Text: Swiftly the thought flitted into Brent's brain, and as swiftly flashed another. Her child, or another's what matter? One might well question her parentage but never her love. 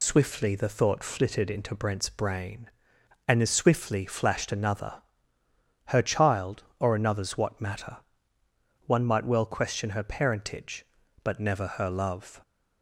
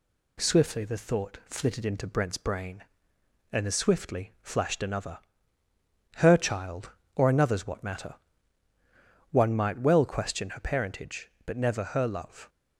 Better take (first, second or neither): second